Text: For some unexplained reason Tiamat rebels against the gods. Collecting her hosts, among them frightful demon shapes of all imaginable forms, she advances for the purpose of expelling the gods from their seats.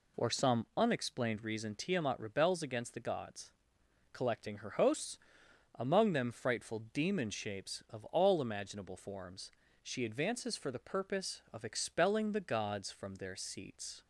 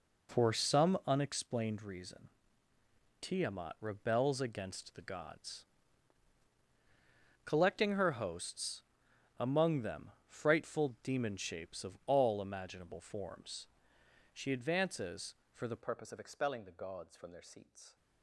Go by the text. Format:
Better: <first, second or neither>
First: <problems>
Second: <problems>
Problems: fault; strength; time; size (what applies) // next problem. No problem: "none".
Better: first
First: none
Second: pauses between "reason" and "Tiamat"; noticeable; at 2.2 s; 0.92 s long // pauses between "them" and "frightful"; slight; at 10.1 s; 0.16 s long // changes voice at "purpose"; from 15.8 s on; 2.1 s long